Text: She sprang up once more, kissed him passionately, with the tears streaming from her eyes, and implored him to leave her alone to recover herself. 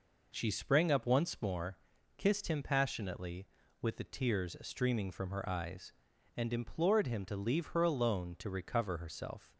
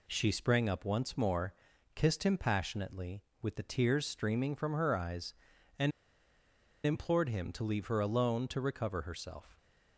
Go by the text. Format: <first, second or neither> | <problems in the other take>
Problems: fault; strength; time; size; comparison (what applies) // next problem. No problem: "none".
first | pauses between "and" and "implored"; noticeable; at 5.9 s; 0.93 s long